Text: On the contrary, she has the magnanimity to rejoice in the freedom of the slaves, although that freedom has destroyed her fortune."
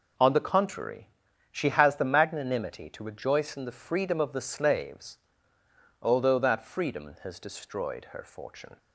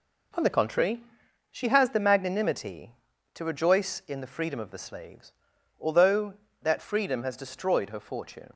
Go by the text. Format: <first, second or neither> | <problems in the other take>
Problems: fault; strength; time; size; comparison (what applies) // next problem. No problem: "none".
neither | none